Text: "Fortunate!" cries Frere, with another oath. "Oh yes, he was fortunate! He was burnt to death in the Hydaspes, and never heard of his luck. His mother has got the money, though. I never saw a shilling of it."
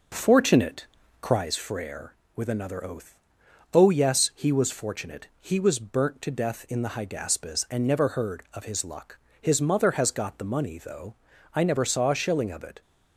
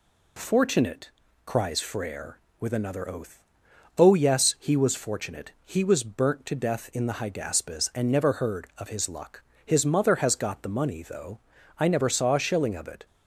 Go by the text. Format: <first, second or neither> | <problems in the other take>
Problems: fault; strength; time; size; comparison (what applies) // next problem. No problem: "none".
second | starts louder than the rest; noticeable; until 1.4 s; 5.5 dB